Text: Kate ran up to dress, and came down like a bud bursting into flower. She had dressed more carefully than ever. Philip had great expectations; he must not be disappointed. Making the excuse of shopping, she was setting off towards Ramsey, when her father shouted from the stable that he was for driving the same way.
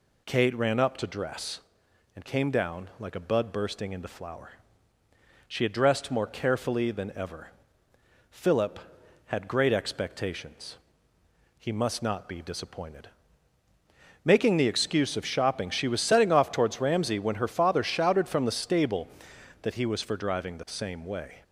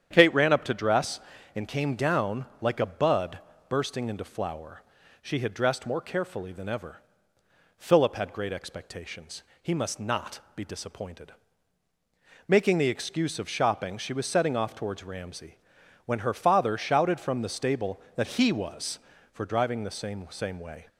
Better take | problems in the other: first | starts louder than the rest; strong; until 1.1 s; 9 dB // pauses between "bud" and "bursting"; slight; at 3.3 s; 0.30 s long // pauses between "not" and "be"; slight; at 10.4 s; 0.16 s long // says "same" twice; at 20.3 s

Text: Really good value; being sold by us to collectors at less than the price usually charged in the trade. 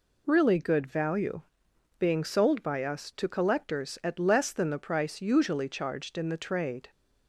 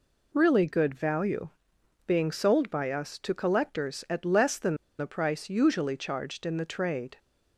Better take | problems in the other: first | pauses between "than" and "the"; slight; at 4.7 s; 0.22 s long

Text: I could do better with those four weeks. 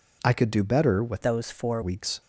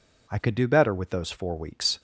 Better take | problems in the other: second | changes voice from "those" to "four"; from 1.2 to 1.8 s; 0.6 s long

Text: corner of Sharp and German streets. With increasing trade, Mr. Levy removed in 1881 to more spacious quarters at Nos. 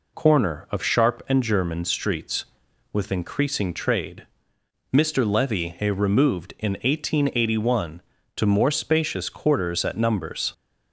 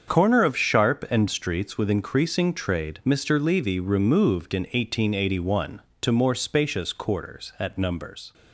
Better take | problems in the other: first | starts louder than the rest; strong; until 1.1 s; 7 dB // skips "German"; at 1.2 s

